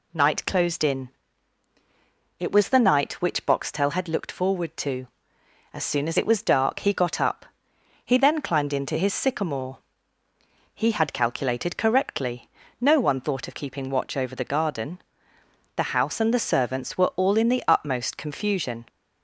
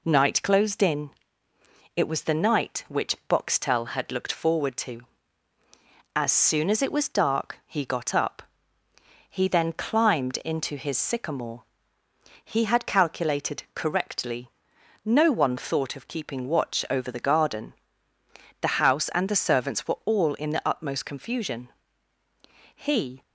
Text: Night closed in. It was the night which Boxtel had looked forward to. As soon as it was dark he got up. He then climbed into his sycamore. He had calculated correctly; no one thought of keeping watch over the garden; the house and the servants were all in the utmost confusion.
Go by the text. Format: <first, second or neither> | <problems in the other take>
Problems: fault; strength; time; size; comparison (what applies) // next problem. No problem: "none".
first | goes on to say "He"; slight; from 22.7 s on; 0.48 s long